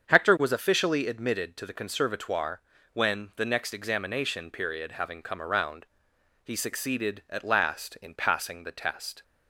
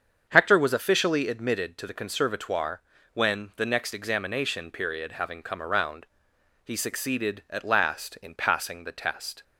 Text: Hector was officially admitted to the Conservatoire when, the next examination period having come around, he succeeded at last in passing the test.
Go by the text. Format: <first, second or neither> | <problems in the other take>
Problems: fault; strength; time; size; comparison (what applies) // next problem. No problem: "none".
neither | starts louder than the rest; strong; the same in both // pauses between "Conservatoire" and "when"; slight; the same in both